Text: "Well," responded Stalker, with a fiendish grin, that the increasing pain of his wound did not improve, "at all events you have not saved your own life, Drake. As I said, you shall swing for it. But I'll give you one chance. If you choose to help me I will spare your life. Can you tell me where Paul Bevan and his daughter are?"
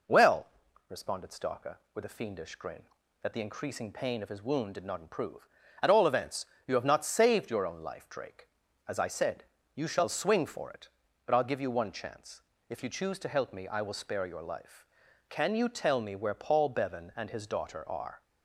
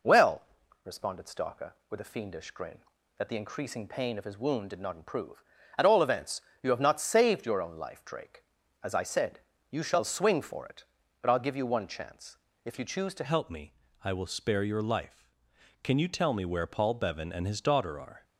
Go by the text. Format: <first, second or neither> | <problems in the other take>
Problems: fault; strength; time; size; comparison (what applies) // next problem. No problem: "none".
first | pauses between "events" and "you"; slight; at 6.3 s; 0.24 s long; slight in the first // changes voice at "help"; from 13.2 s on; 5.0 s long // pauses between "me" and "I"; slight; at 13.7 s; 0.30 s long